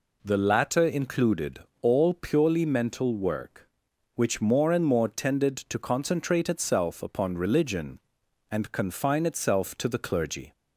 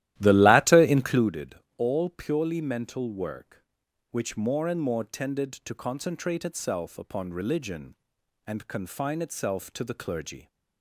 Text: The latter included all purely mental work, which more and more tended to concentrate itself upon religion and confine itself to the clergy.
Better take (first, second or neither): first